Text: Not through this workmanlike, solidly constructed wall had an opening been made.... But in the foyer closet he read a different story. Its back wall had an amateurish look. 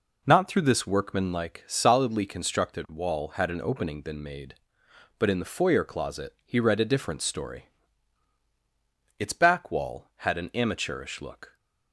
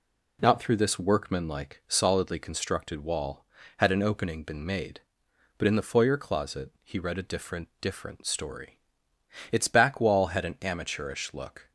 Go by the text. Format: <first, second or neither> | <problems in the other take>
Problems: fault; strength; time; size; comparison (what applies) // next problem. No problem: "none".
first | says "different" twice; at 7.8 s